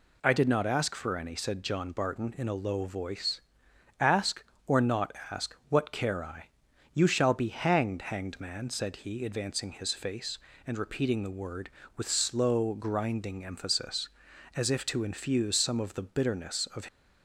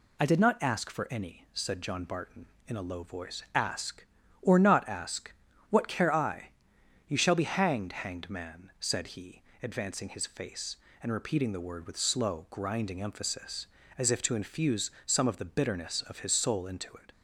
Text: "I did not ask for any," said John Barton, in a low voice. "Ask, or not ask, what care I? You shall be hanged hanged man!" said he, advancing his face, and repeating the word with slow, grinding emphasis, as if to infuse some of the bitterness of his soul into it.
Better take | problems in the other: second | pauses between "not" and "ask"; slight; at 5.1 s; 0.16 s long // stops before "his soul into it"; at 16.8 s

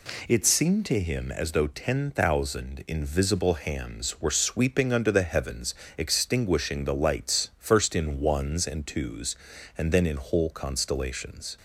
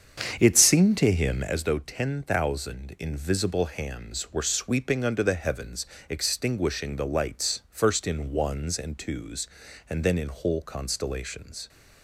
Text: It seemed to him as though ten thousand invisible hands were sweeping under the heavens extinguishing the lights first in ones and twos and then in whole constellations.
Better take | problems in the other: first | starts louder than the rest; strong; until 1.7 s; 7.5 dB // pauses between "heavens" and "extinguishing"; slight; at 5.8 s; 0.22 s long; slight in the first

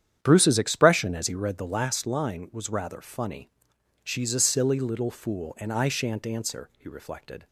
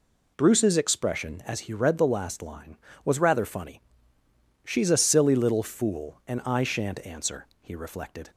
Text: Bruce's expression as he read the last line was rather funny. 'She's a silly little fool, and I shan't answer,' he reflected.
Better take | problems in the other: second | starts louder than the rest; strong; until 1.9 s; 9.5 dB

